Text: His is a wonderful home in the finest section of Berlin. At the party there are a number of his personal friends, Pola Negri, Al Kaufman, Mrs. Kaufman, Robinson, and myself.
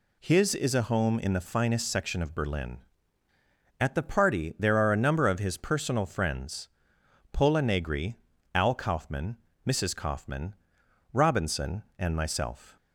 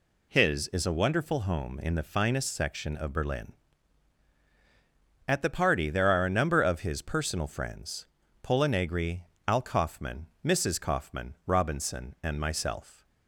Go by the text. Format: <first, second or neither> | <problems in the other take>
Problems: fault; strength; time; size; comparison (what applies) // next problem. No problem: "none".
second | skips "wonderful"; at 0.8 s